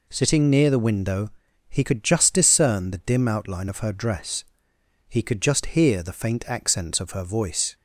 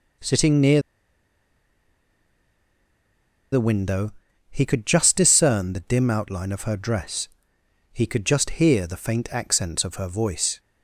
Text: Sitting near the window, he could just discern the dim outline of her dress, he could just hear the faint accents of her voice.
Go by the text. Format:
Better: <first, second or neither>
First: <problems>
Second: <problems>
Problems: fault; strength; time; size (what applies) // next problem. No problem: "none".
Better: first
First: none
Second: pauses between "near" and "the"; strong; at 0.8 s; 2.7 s long